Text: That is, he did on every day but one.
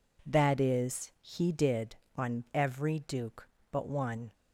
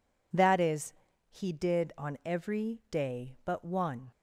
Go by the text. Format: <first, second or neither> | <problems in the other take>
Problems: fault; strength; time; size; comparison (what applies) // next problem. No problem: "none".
second | says "duke" for "day"; at 2.9 s